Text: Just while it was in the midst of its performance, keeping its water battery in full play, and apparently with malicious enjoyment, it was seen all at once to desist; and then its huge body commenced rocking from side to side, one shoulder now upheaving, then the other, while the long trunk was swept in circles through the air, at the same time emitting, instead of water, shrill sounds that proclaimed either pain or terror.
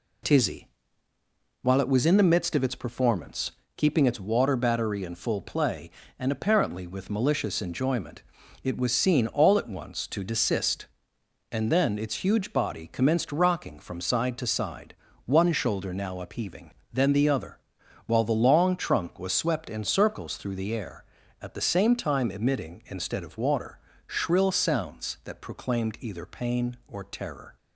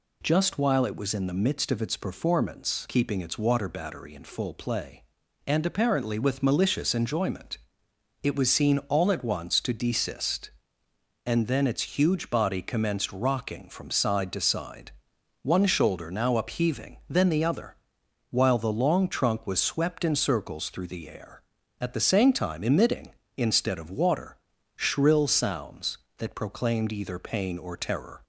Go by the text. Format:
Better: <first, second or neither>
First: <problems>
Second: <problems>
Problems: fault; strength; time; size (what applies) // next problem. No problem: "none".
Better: second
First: says "Tizzy" for "Just"; at 0.2 s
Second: none